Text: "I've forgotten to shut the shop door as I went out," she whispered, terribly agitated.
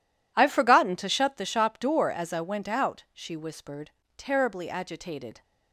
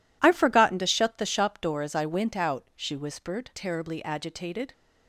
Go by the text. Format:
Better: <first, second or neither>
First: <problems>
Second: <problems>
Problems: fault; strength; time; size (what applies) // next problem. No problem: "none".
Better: neither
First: none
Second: none